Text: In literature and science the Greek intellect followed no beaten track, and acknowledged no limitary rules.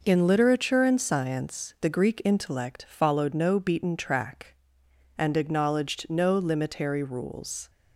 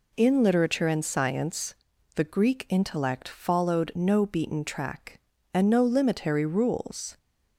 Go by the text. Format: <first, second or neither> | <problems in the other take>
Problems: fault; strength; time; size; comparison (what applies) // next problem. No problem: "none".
first | pauses between "science" and "the"; at 1.7 s; 0.44 s long // skips "acknowledged"; at 5.7 s